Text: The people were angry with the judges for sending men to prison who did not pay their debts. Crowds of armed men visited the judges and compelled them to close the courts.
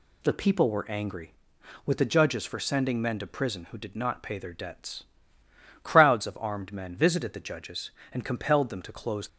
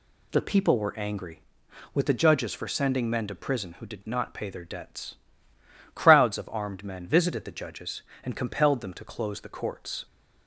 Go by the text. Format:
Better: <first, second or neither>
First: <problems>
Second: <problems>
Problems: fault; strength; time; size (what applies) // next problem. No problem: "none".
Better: second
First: stops before "the courts"; at 9.2 s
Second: none